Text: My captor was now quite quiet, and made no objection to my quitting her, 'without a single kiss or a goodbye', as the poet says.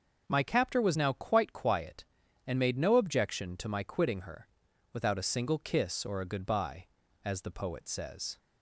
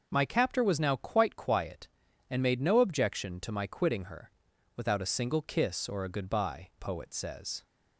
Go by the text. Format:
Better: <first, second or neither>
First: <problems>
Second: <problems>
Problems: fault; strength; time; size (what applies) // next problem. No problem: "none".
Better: first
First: none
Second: skips "as the"; at 6.7 s